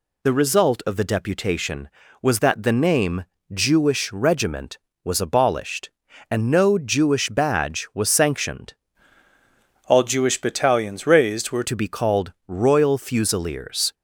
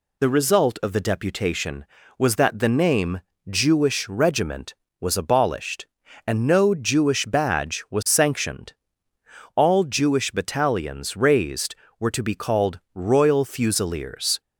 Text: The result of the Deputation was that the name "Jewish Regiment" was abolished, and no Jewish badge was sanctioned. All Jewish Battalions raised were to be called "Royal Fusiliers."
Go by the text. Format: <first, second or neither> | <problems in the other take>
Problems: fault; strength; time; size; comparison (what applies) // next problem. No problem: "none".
second | pauses between "name" and "Jewish"; slight; at 3.2 s; 0.30 s long; slight in the second // changes voice from "All" to "were"; from 9.8 to 11.6 s; 1.8 s long // pauses between "called" and "Royal"; slight; at 12.3 s; 0.16 s long; slight in the second